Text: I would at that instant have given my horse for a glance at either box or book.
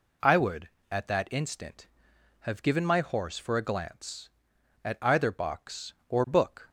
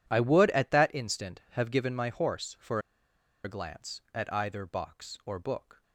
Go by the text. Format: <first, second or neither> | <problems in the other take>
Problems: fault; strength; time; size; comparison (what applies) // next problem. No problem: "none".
first | pauses between "for" and "a"; noticeable; at 2.7 s; 0.65 s long